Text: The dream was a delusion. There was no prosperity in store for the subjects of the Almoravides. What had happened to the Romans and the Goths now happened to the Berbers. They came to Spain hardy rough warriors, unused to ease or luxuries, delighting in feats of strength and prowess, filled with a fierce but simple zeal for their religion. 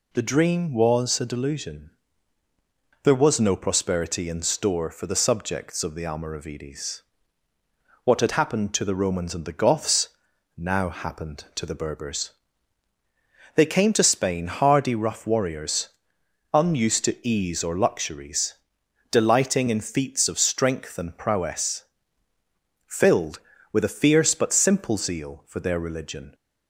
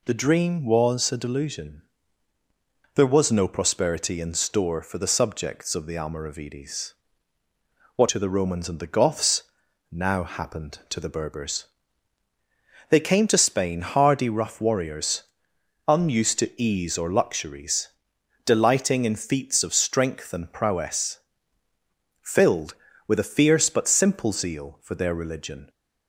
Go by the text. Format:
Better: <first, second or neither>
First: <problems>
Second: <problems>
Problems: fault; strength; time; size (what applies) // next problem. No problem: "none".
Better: first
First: pauses between "Goths" and "now"; noticeable; at 10.0 s; 0.48 s long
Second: skips "had happened"; at 8.0 s // pauses between "Goths" and "now"; noticeable; at 9.4 s; 0.48 s long